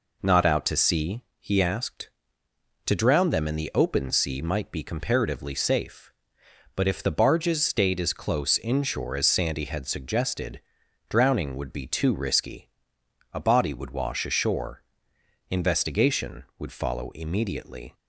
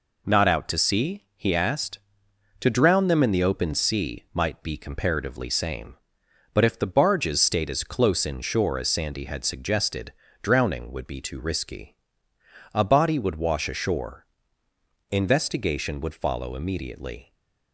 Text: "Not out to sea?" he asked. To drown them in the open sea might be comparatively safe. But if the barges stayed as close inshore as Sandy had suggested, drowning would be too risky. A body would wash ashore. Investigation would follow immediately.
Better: first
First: none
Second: says "same" for "safe"; at 5.4 s

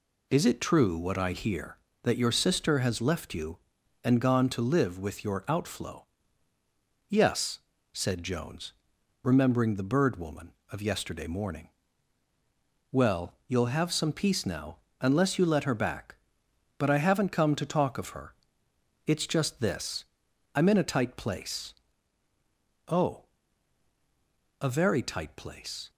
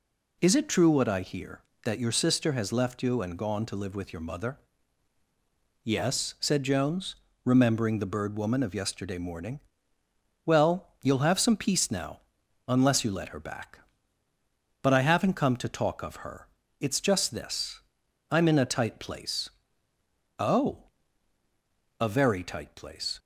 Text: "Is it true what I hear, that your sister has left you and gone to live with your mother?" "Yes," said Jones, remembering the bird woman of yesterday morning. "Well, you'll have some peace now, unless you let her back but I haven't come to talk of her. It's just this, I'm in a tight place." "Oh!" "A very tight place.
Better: second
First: says "outflow" for "mother"; at 5.4 s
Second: none

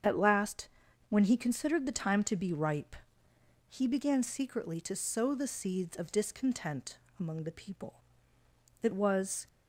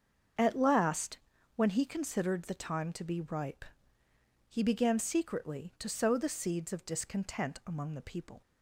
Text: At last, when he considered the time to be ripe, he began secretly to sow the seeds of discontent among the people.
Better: second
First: starts louder than the rest; strong; until 1.4 s; 7.5 dB // pauses between "discontent" and "among"; slight; at 6.9 s; 0.22 s long // goes on to say "It was"; noticeable; from 8.8 s on; 0.64 s long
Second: starts louder than the rest; until 1.7 s; 7 dB

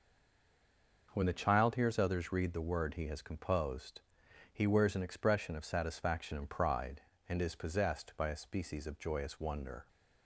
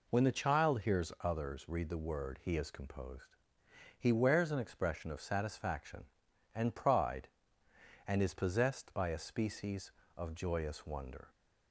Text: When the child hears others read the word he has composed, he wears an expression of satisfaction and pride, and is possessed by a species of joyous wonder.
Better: second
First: stays silent before the first word; until 1.0 s; 1.0 s long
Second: none

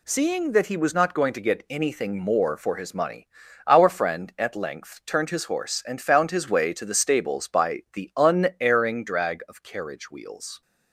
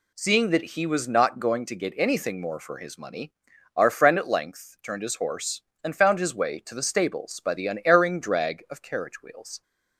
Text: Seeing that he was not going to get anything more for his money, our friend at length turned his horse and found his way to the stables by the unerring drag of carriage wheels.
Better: neither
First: none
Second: none

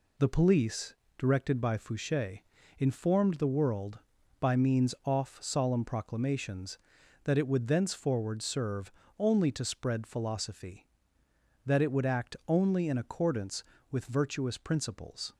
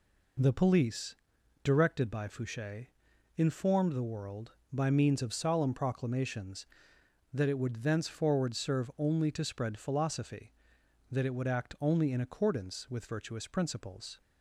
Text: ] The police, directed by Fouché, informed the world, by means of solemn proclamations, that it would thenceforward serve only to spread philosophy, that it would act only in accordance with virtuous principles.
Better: second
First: says "off" for "of"; at 5.0 s // pauses between "serve" and "only"; slight; at 8.9 s; 0.26 s long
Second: none

